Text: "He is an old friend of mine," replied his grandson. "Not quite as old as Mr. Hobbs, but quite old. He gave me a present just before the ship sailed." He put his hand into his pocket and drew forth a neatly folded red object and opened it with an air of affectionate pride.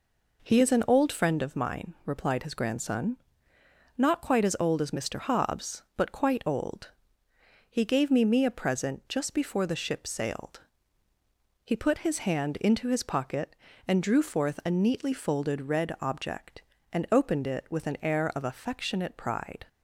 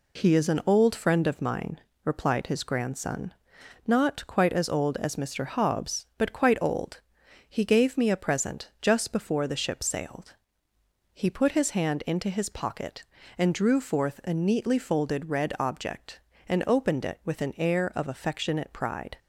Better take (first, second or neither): second